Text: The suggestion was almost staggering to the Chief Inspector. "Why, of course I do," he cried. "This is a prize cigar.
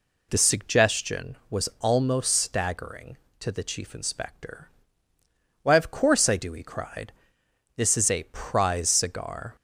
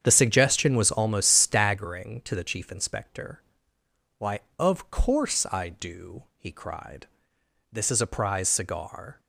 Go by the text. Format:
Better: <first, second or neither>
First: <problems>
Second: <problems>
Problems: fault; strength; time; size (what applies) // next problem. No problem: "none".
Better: first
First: none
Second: starts louder than the rest; strong; until 1.8 s; 8 dB